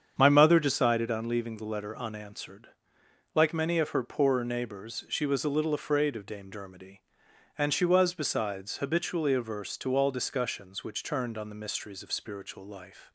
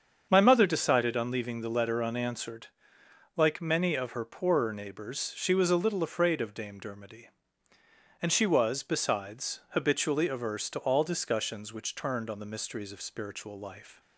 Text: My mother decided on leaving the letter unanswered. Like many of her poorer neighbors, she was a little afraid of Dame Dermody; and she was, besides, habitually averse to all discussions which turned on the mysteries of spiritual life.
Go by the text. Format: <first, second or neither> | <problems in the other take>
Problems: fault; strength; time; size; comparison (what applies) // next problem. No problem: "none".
neither | starts louder than the rest; strong; the same in both